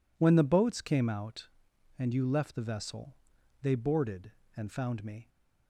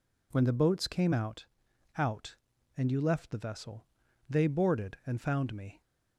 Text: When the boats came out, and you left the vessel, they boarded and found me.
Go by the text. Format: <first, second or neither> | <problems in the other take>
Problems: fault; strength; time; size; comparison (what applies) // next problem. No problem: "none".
first | says "out" twice; at 1.9 s